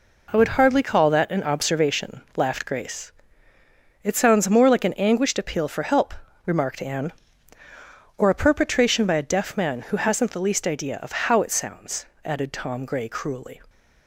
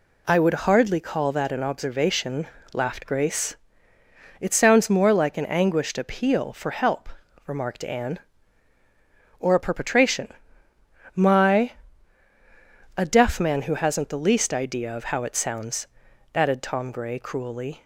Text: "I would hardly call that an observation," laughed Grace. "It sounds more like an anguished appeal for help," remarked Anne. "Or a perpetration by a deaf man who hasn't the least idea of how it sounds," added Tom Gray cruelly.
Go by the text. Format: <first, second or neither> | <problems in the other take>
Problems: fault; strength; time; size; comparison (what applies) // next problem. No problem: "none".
first | says "my" for "by"; at 11.1 s